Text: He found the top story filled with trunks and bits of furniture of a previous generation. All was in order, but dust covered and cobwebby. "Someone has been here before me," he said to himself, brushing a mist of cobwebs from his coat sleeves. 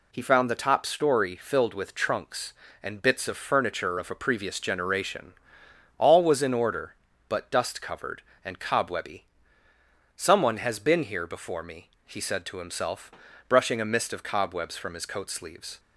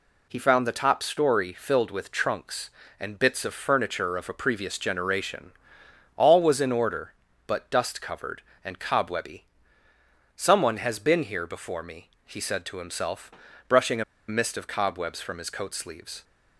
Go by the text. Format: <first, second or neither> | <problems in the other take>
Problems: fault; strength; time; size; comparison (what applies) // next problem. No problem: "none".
first | pauses between "a" and "mist"; slight; at 14.0 s; 0.25 s long